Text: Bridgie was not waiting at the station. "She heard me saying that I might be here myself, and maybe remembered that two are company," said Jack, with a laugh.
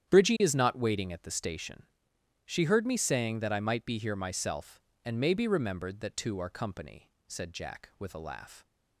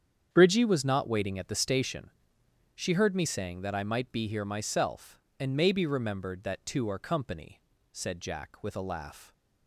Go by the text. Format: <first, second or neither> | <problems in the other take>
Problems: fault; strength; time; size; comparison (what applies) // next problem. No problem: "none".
second | starts louder than the rest; strong; until 1.1 s; 10 dB; strong in the second // says "is" for "was"; at 0.4 s